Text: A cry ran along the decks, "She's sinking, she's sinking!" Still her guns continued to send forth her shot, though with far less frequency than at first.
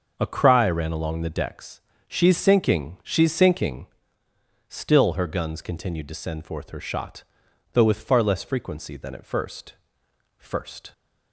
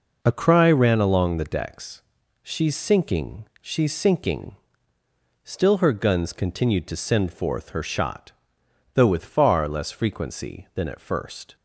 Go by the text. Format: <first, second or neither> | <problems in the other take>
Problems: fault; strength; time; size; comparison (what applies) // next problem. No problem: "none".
second | starts louder than the rest; until 1.1 s; 6.5 dB // says "first" twice; at 10.3 s